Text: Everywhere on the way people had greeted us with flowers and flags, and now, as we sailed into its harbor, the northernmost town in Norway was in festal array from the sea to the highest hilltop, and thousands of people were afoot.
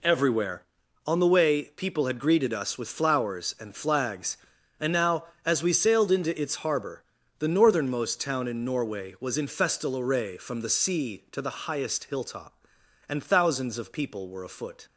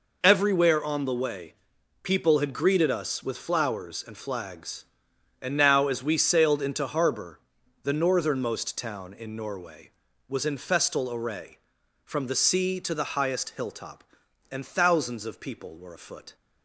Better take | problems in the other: first | pauses between "way" and "people"; noticeable; at 1.5 s; 0.48 s long // skips "its"; at 6.8 s

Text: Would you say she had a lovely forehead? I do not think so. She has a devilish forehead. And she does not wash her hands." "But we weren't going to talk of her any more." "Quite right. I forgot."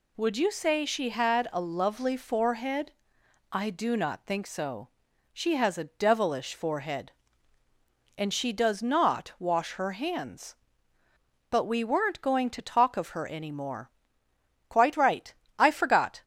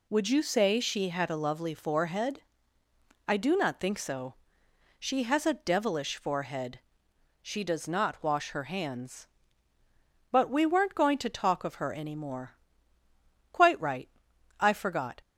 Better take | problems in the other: first | skips "And"; at 7.1 s

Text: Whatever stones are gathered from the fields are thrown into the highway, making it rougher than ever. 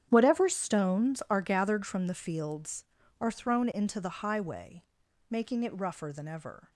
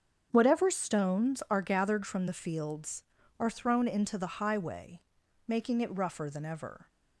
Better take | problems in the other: second | gets quieter; strong; throughout; 15.5 dB // starts louder than the rest; strong; until 1.0 s; 9.5 dB; strong in the second

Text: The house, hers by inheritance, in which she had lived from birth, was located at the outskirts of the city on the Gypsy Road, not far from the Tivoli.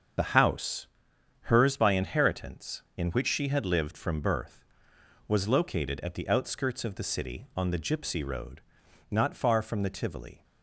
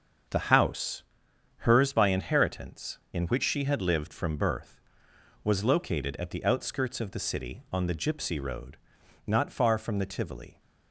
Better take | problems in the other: second | loses the start of "The"; at 0.1 s; 45 ms // starts louder than the rest; until 1.7 s; 7 dB; also in the second

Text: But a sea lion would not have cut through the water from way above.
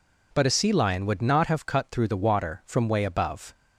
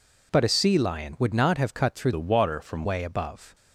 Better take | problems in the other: first | changes voice from "the" to "from"; from 2.1 to 2.8 s; 0.7 s long

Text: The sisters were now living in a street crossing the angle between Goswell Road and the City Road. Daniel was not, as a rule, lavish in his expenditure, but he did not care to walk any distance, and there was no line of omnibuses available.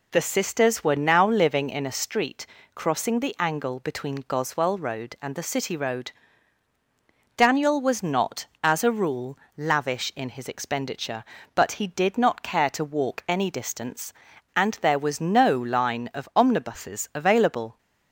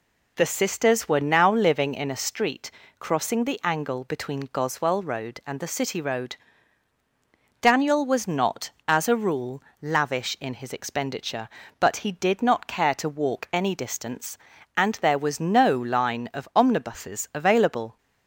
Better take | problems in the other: neither | pauses between "street" and "crossing"; slight; the same in both

